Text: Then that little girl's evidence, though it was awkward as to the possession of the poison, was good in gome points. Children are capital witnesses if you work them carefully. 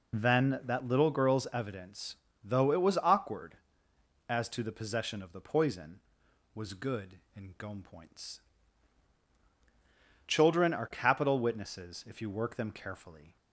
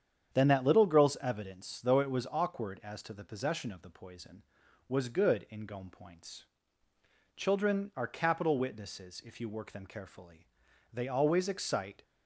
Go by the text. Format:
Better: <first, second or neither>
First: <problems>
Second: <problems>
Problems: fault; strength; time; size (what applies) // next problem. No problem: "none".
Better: first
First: none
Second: starts louder than the rest; strong; until 1.3 s; 8.5 dB // goes on to say "They always excite"; noticeable; from 10.9 s on; 1.1 s long